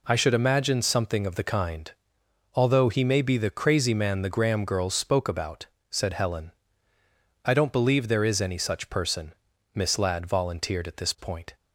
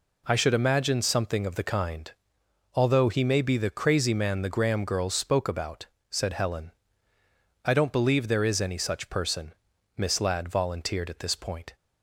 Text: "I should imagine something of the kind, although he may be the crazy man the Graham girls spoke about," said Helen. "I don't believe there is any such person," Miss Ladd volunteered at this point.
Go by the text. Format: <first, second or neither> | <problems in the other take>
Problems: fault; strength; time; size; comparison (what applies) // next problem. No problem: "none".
neither | none